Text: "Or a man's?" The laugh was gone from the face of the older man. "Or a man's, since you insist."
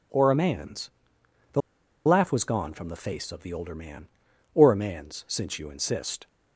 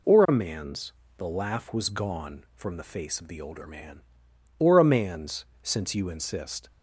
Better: second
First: pauses between "The" and "laugh"; noticeable; at 1.6 s; 0.46 s long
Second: none

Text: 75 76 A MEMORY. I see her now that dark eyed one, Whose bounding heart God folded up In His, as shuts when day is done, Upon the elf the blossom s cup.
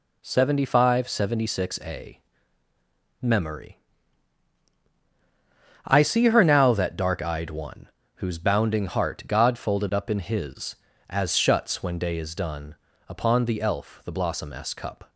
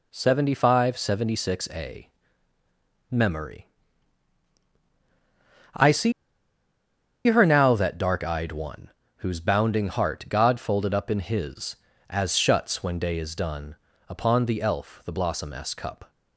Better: first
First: pauses between "A" and "MEMORY"; at 2.2 s; 1.0 s long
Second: pauses between "A" and "MEMORY"; at 2.0 s; 1.0 s long // pauses between "see" and "her"; at 6.1 s; 1.1 s long

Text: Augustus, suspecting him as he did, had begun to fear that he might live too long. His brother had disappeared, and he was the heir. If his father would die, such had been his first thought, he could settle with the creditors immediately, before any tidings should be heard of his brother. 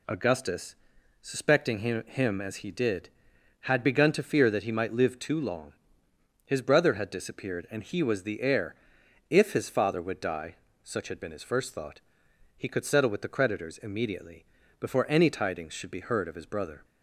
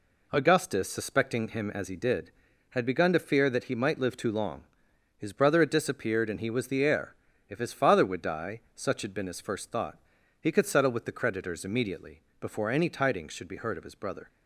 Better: second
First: says "him" twice; at 2.0 s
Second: none

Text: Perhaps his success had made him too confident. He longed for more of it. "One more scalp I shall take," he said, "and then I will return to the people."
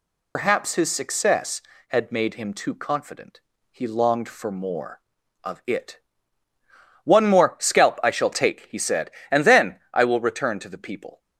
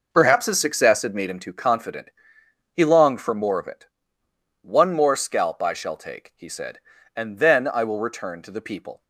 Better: second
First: loses the start of "Perhaps"; at 0.3 s; 100 ms // pauses between "then" and "I"; slight; at 9.7 s; 0.16 s long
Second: none

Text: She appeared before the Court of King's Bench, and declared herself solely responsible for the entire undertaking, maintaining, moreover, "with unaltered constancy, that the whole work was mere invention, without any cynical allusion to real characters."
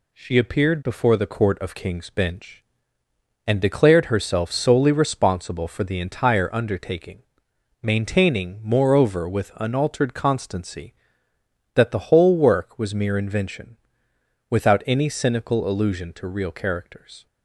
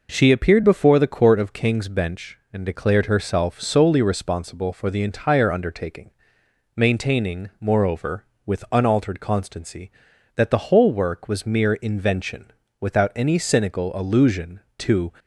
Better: first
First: none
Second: stops before "real characters"; at 15.1 s

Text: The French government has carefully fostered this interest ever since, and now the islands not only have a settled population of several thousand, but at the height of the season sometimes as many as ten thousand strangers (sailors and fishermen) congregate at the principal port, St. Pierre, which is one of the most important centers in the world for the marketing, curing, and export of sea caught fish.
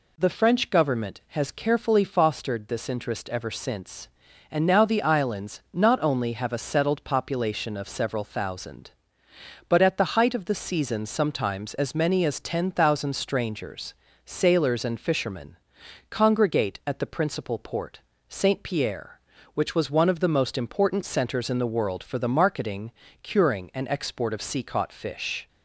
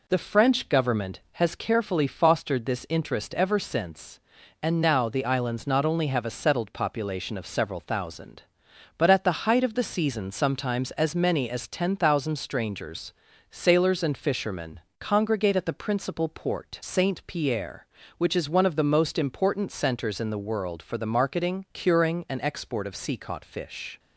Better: second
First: says "was" for "is"; at 19.7 s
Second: none

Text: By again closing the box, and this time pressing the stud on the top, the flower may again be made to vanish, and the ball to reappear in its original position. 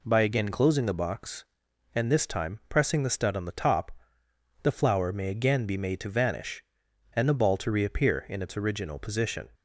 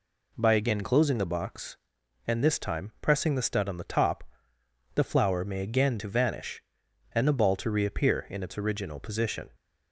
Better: first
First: none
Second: skips "be made"; at 5.9 s

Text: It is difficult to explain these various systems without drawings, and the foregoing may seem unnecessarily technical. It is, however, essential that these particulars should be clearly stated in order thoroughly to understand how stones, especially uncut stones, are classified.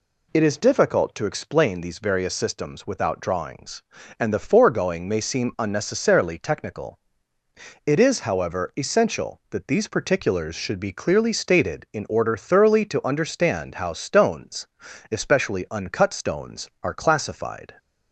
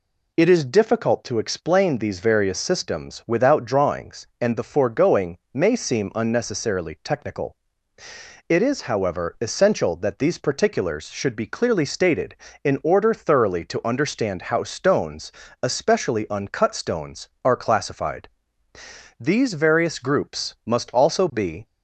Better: first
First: none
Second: pauses between "foregoing" and "may"; slight; at 5.3 s; 0.16 s long // goes on to say "These various groups must also be"; strong; from 19.1 s on; 2.4 s long

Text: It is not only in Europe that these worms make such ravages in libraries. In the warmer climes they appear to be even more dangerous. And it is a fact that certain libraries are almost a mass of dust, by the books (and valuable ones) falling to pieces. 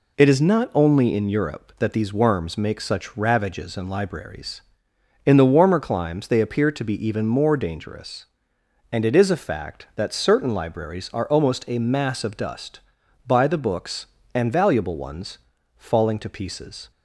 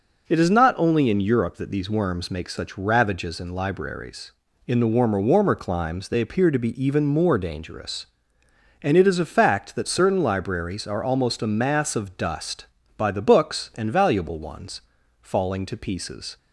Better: first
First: none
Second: says "warmer" twice; at 5.2 s

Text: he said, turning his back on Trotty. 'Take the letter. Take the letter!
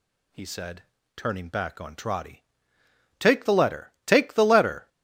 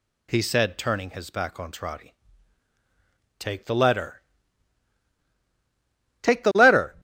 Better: second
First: skips "his"; at 1.4 s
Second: none

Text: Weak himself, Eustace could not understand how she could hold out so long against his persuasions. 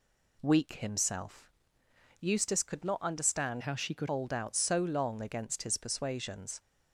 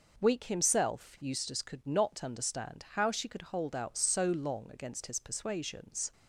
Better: second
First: changes voice from "how" to "could"; from 3.6 to 4.0 s; 0.4 s long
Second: none

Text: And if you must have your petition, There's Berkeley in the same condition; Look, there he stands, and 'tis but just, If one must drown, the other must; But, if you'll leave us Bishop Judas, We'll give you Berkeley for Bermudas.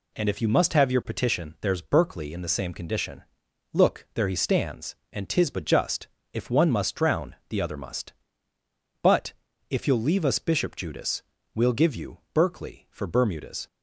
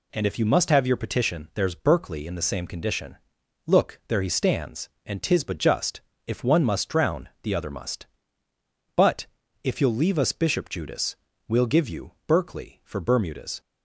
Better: neither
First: none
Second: none

